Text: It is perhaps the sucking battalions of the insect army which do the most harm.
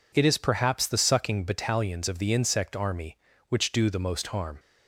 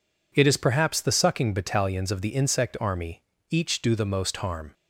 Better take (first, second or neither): first